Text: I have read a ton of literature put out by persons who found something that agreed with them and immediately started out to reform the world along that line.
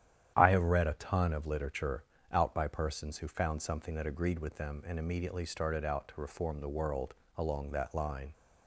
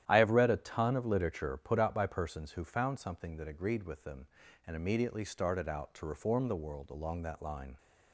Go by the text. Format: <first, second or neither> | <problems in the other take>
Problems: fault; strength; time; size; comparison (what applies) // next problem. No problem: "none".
second | starts louder than the rest; strong; until 1.3 s; 10.5 dB; strong in the second // skips "put"; at 2.1 s // pauses between "world" and "along"; slight; at 7.1 s; 0.24 s long